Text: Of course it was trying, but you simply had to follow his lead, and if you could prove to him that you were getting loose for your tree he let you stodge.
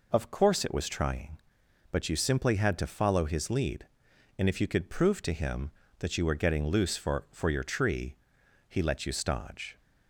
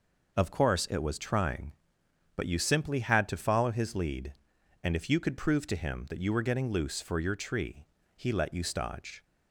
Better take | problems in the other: second | says "for" twice; at 7.3 s // pauses between "tree" and "he"; noticeable; at 8.1 s; 0.52 s long; slight in the second

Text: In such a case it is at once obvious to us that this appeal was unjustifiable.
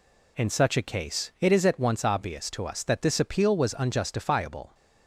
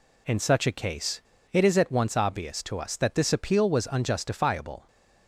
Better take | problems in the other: first | pauses between "case" and "it"; slight; at 1.2 s; 0.31 s long

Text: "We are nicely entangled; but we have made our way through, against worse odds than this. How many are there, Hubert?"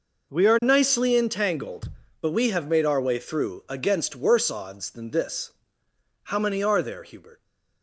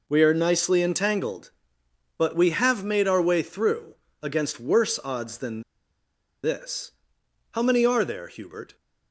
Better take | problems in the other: first | pauses between "than" and "this"; noticeable; at 5.6 s; 0.83 s long

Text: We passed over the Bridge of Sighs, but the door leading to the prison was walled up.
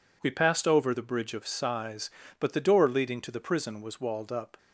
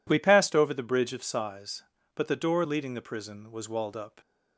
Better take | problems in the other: first | skips "to"; at 2.9 s

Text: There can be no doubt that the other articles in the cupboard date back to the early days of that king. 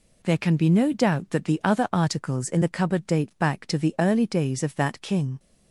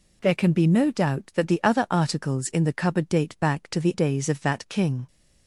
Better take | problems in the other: first | skips "early"; at 3.9 s

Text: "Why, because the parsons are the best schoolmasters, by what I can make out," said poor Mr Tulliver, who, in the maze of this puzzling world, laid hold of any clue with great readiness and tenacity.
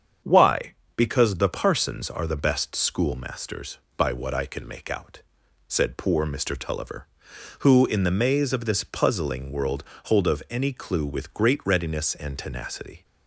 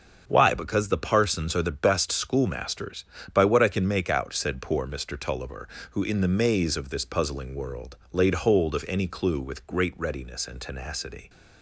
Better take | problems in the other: second | starts louder than the rest; strong; until 1.4 s; 7.5 dB; also in the second // skips "laid"; at 9.9 s

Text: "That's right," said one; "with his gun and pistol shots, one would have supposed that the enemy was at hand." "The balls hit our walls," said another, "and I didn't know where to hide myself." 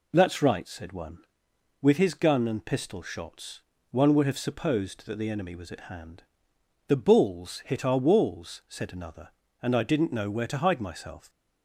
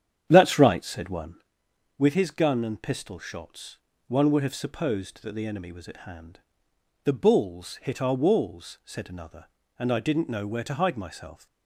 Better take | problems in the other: first | starts louder than the rest; strong; until 1.4 s; 9.5 dB

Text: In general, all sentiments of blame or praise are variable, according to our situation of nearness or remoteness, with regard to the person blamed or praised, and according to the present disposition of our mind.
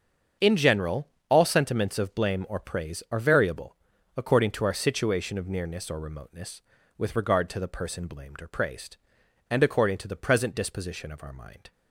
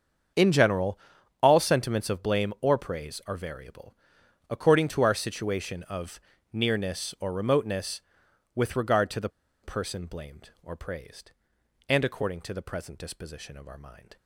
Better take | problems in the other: first | starts louder than the rest; strong; until 1.8 s; 7 dB; strong in the first // pauses between "of" and "nearness"; slight; at 6.1 s; 0.32 s long // pauses between "the" and "person"; slight; at 9.2 s; 0.33 s long

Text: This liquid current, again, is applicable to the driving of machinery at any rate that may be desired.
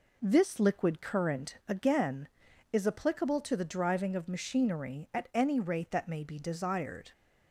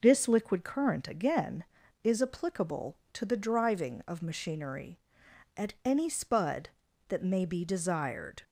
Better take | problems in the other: first | says "spud" for "rate"; at 6.0 s

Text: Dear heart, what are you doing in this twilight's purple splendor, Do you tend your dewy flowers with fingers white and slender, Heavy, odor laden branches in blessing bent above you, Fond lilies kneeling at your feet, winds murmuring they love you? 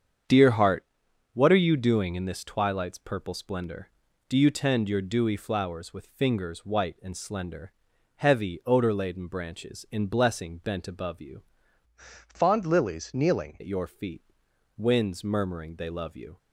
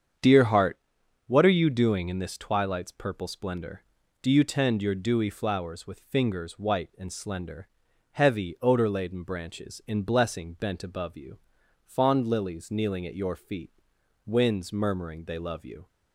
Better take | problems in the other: second | starts louder than the rest; strong; until 1.7 s; 7.5 dB; strong in the second // changes voice from "Fond" to "kneeling"; from 12.2 to 13.5 s; 1.3 s long

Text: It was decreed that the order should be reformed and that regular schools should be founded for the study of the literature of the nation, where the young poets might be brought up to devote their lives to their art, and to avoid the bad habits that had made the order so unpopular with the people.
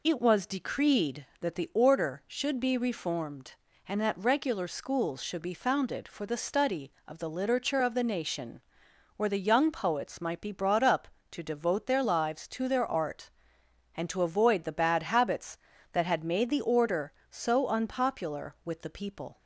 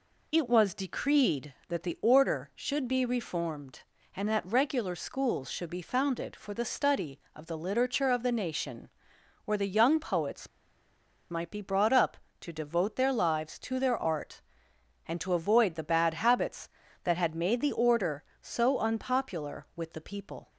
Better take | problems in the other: first | pauses between "poets" and "might"; noticeable; at 10.4 s; 0.81 s long

